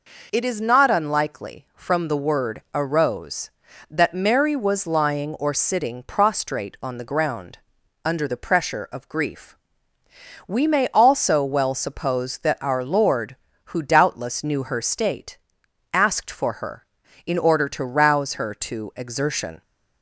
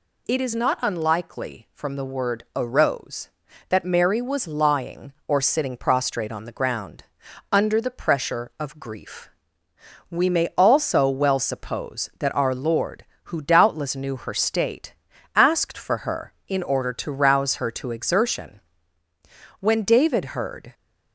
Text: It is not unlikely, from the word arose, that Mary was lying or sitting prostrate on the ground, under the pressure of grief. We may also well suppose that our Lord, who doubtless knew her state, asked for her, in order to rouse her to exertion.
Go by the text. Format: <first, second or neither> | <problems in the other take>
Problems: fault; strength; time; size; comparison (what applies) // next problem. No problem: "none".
first | goes on to say "When David heard"; noticeable; from 19.5 s on; 1.1 s long